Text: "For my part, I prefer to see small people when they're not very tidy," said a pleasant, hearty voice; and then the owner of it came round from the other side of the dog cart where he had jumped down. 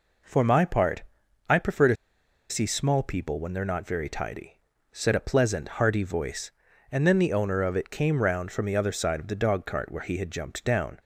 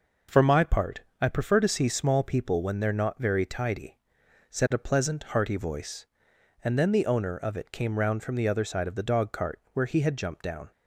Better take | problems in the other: second | pauses between "to" and "see"; noticeable; at 1.9 s; 0.55 s long

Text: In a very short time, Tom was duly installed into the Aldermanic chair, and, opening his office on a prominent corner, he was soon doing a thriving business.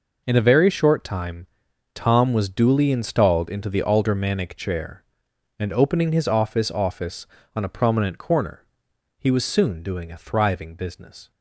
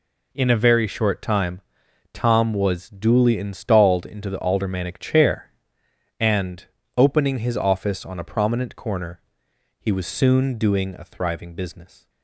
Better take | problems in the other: second | says "office" twice; at 6.7 s

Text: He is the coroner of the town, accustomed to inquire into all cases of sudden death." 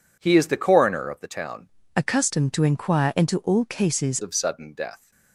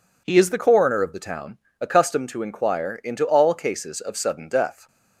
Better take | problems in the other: second | changes voice from "accustomed" to "cases"; from 1.9 to 4.1 s; 2.2 s long

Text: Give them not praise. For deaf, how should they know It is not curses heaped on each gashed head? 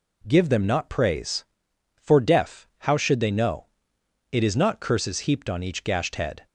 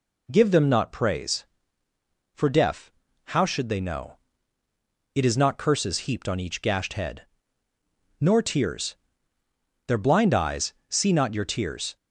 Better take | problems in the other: first | pauses between "know" and "It"; noticeable; at 4.1 s; 0.98 s long; noticeable in the first // goes on to say "Nor tears Their blind eyes see not your tears"; strong; from 8.2 s on; 3.7 s long

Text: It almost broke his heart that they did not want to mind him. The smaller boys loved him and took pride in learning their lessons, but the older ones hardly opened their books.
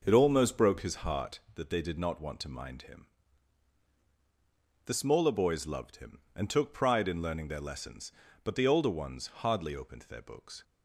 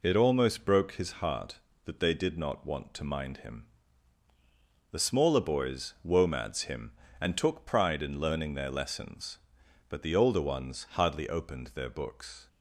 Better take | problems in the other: first | says "womads" for "loved"; at 6.0 s

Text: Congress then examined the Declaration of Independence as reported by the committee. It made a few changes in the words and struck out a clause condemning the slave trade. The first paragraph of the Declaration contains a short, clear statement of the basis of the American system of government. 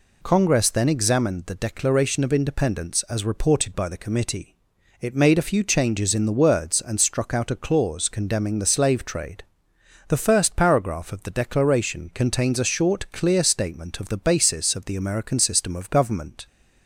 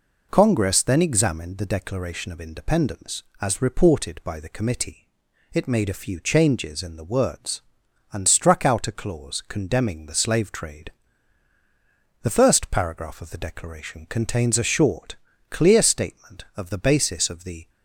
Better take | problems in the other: first | stops before "American system of government"; at 17.6 s

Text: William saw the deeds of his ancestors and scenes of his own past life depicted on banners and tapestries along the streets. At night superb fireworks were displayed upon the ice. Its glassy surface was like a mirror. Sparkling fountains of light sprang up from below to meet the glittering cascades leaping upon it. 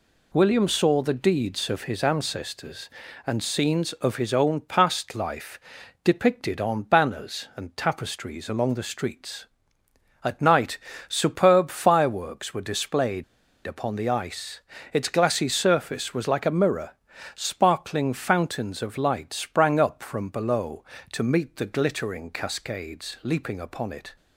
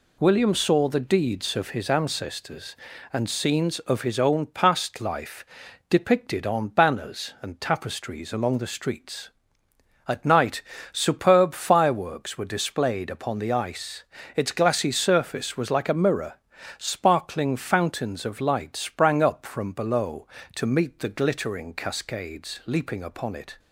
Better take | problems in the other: second | pauses between "life" and "depicted"; at 5.5 s; 0.44 s long; also in the second // pauses between "night" and "superb"; slight; at 10.7 s; 0.28 s long; slight in the second // pauses between "displayed" and "upon"; at 13.2 s; 0.43 s long

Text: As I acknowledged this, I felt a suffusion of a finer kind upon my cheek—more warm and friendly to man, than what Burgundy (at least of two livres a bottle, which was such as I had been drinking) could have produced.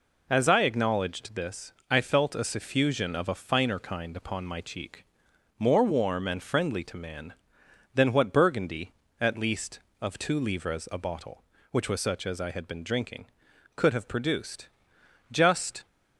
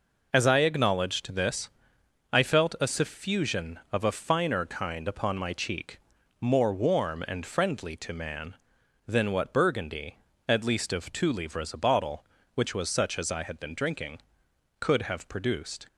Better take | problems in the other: second | goes on to say "Just"; from 15.3 s on; 0.54 s long

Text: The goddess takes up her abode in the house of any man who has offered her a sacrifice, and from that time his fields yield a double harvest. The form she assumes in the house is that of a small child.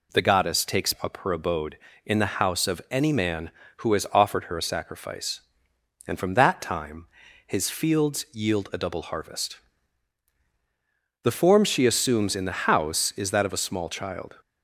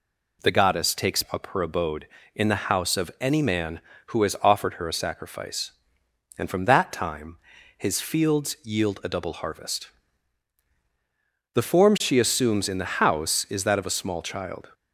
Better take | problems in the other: neither | pauses between "time" and "his"; the same in both

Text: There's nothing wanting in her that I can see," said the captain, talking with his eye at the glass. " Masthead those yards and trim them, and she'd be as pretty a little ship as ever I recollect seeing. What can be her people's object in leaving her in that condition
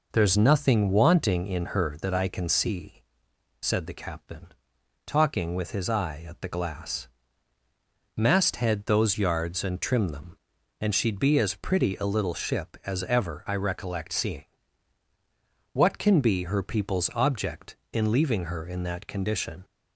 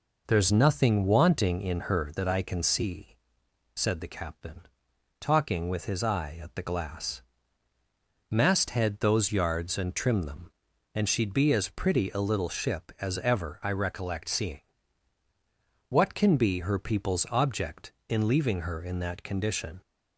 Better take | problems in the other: neither | none

